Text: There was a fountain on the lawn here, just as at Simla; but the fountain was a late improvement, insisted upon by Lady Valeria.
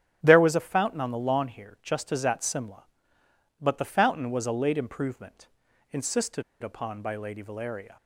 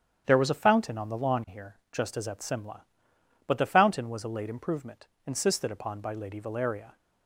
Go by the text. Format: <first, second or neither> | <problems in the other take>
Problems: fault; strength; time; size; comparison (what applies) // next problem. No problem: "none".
second | starts louder than the rest; strong; until 1.2 s; 10.5 dB; strong in the second // pauses between "insisted" and "upon"; slight; at 6.4 s; 0.19 s long